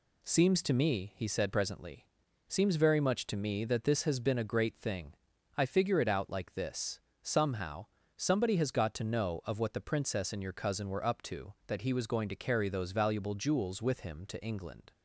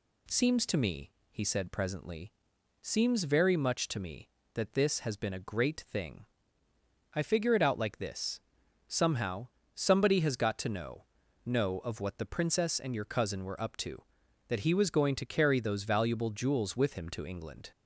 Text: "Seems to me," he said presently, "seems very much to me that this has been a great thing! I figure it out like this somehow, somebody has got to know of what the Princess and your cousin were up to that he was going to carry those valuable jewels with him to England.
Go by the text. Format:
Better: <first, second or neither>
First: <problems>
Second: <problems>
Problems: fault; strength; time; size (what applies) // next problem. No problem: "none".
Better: first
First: pauses between "this" and "somehow"; slight; at 6.9 s; 0.24 s long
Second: pauses between "this" and "somehow"; noticeable; at 8.4 s; 0.48 s long // says "know" twice; at 11.4 s